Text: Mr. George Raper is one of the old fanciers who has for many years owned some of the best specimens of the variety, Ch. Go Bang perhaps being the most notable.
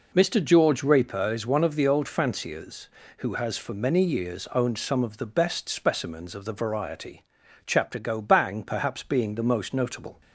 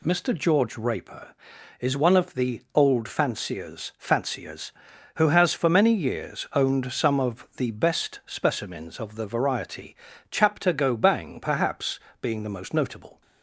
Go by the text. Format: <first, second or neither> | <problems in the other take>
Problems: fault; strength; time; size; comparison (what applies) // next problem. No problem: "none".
first | says "fanciers" twice; at 3.9 s // pauses between "perhaps" and "being"; slight; at 12.0 s; 0.20 s long